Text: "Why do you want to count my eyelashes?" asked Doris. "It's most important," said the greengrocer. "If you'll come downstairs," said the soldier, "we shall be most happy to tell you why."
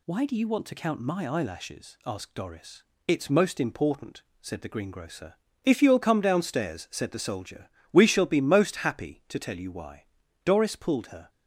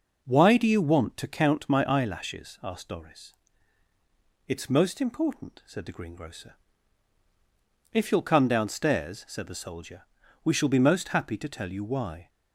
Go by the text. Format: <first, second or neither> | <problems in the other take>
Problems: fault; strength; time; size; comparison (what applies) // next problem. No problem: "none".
second | goes on to say "Doris pulled her"; noticeable; from 10.4 s on; 0.86 s long